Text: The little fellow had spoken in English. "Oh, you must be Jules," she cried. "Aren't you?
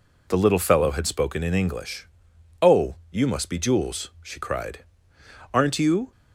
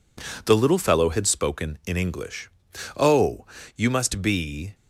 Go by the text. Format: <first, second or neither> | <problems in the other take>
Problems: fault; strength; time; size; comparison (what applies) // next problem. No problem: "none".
first | stops before "Jules she cried Aren't you"; at 4.7 s